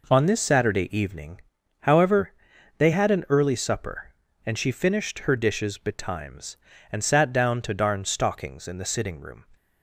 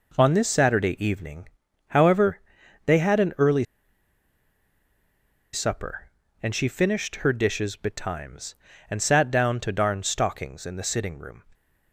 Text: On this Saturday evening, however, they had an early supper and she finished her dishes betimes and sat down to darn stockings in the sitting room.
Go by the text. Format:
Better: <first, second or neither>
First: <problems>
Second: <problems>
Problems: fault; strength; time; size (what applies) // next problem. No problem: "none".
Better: first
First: none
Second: pauses between "early" and "supper"; strong; at 3.6 s; 1.8 s long